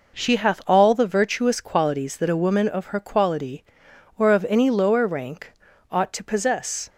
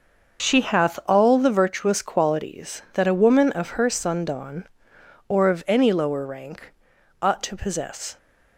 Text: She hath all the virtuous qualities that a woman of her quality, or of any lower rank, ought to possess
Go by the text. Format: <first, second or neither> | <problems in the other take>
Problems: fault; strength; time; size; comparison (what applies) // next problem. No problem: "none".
first | starts louder than the rest; until 1.5 s; 6 dB // says "sundawn" for "quality"; at 3.9 s